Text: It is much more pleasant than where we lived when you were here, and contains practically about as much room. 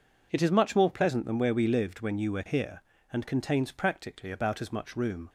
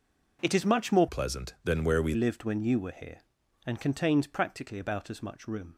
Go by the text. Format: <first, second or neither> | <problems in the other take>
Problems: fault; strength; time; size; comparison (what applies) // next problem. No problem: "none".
first | changes voice from "pleasant" to "we"; from 1.0 to 2.1 s; 1.1 s long